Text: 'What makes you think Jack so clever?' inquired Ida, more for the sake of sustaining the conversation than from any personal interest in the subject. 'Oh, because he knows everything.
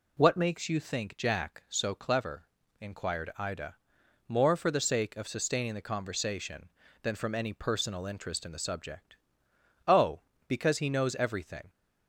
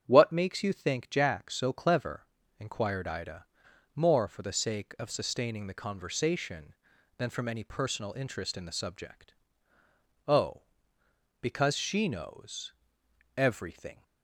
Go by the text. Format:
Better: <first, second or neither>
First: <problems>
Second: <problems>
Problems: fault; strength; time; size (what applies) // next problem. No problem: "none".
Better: first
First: none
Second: starts louder than the rest; strong; until 1.0 s; 8.5 dB // says "she" for "he"; at 11.7 s // pauses between "knows" and "everything"; noticeable; at 12.7 s; 0.64 s long